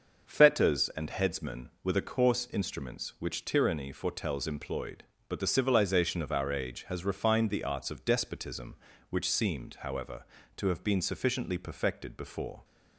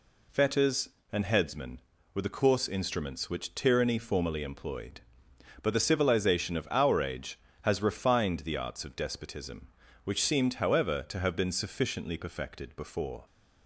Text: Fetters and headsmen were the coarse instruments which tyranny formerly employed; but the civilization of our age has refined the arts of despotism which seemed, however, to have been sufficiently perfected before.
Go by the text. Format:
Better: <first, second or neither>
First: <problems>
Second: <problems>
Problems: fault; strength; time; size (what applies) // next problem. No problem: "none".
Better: second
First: starts louder than the rest; until 1.2 s; 6.5 dB // says "foretells" for "formerly"; at 3.9 s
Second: none